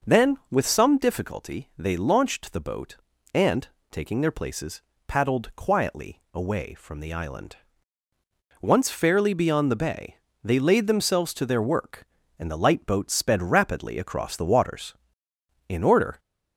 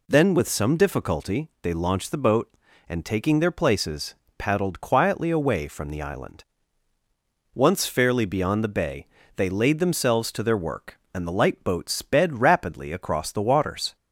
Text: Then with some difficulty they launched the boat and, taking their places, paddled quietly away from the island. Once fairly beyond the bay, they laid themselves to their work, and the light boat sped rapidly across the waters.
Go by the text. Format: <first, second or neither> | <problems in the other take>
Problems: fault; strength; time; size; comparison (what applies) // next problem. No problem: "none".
second | goes on to say "In order"; from 15.6 s on; 0.50 s long